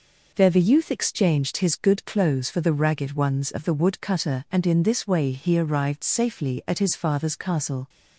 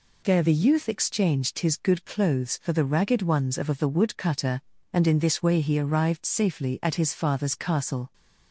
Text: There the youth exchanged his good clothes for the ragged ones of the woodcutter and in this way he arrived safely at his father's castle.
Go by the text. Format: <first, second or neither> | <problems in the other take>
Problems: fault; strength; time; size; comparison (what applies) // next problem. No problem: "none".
first | says "of" twice; at 3.6 s